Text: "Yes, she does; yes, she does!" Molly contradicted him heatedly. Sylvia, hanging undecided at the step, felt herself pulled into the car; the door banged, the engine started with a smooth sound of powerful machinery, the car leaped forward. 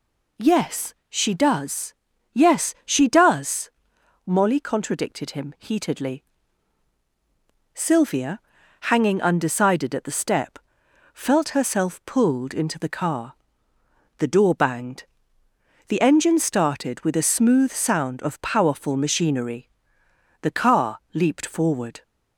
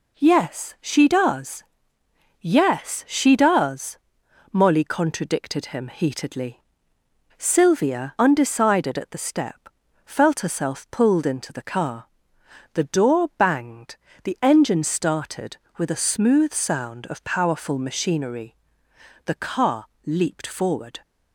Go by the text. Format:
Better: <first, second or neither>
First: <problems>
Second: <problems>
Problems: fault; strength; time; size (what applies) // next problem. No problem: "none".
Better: first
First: none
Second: skips "hanging"; at 8.1 s // pauses between "car" and "leaped"; slight; at 19.8 s; 0.18 s long